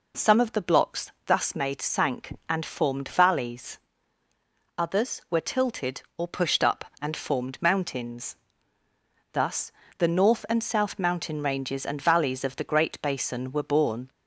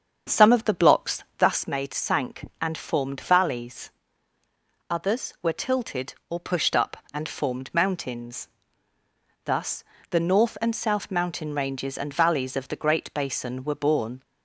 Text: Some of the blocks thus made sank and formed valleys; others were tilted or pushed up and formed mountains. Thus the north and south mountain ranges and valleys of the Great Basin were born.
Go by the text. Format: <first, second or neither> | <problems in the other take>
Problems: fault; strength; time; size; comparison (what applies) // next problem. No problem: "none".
first | starts louder than the rest; until 1.7 s; 7 dB // pauses between "Thus" and "the"; slight; at 9.8 s; 0.26 s long; slight in the first